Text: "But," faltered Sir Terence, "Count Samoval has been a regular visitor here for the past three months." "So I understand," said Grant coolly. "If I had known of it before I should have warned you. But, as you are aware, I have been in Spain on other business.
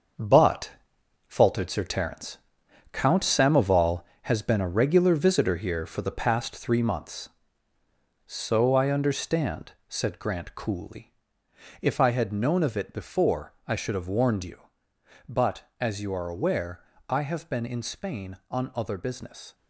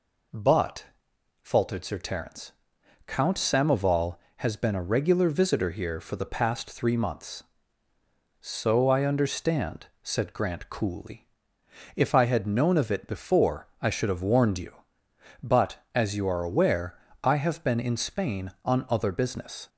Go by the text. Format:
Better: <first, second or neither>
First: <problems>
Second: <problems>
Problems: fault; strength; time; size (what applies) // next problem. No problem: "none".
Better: second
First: gets quieter; strong; throughout; 8.5 dB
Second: none